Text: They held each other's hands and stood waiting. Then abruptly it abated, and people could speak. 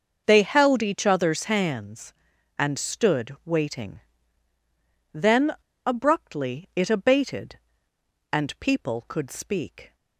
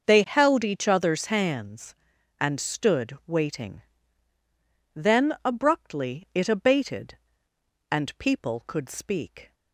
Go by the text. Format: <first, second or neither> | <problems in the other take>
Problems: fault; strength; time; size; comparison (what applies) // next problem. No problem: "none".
second | starts louder than the rest; until 1.2 s; 6 dB; also in the second // pauses between "Then" and "abruptly"; slight; at 5.5 s; 0.34 s long